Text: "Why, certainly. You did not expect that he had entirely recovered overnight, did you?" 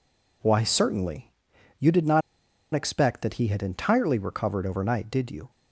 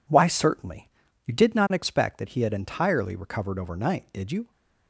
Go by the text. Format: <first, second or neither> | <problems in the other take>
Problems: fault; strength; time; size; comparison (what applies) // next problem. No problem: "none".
second | pauses between "not" and "expect"; noticeable; at 2.2 s; 0.53 s long